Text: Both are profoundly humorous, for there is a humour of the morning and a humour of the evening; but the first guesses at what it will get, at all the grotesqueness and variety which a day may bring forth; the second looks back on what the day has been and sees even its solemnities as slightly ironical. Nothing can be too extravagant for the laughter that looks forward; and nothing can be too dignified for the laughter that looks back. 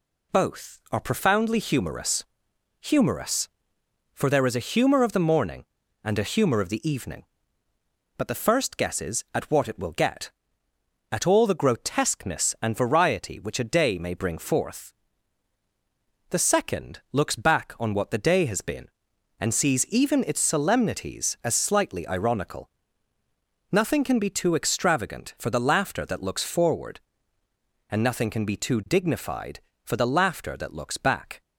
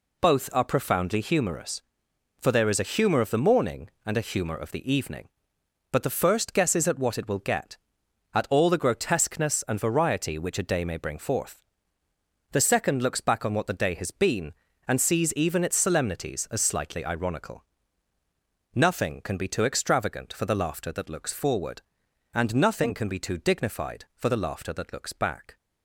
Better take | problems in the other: second | says "humorous" twice; at 2.7 s

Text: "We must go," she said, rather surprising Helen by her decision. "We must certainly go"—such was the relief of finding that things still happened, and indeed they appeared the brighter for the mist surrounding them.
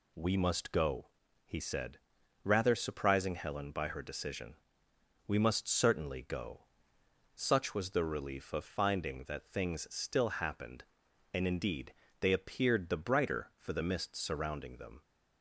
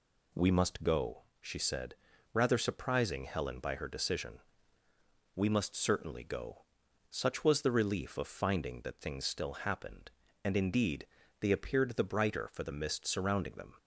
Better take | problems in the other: second | says "he" for "she"; at 1.4 s // pauses between "indeed" and "they"; slight; at 11.9 s; 0.26 s long; slight in the second

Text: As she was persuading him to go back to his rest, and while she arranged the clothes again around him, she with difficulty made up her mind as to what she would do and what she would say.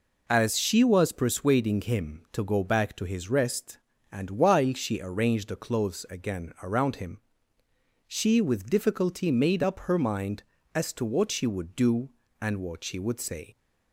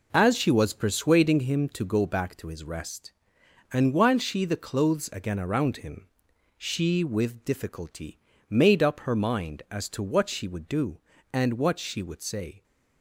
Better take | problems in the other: first | skips "arranged"; at 4.4 s // pauses between "difficulty" and "made"; slight; at 8.1 s; 0.30 s long

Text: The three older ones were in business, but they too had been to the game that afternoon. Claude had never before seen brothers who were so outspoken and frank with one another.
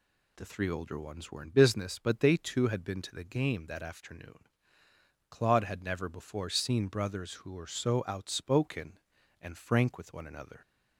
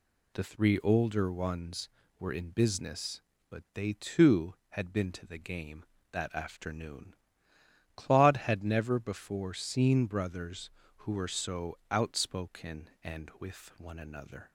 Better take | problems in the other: first | skips "frank"; at 13.3 s

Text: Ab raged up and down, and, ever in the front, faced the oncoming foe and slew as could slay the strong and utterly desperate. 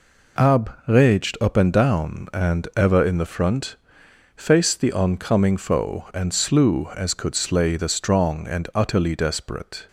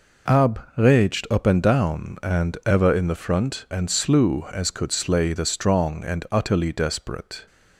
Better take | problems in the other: first | skips "faced the oncoming foe"; at 3.6 s

